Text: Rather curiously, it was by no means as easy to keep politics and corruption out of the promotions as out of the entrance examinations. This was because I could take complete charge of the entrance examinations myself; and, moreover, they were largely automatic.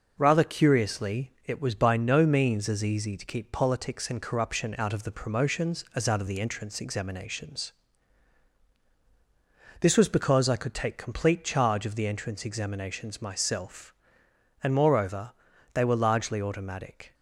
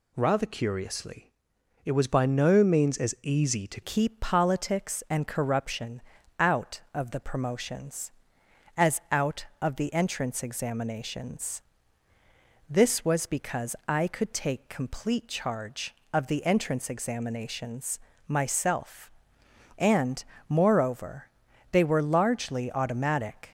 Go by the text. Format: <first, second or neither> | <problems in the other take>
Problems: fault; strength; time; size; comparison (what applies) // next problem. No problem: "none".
first | changes voice at "keep"; from 3.8 s on; 19.7 s long // pauses between "corruption" and "out"; slight; at 6.0 s; 0.36 s long // pauses between "examinations" and "myself"; slight; at 17.9 s; 0.28 s long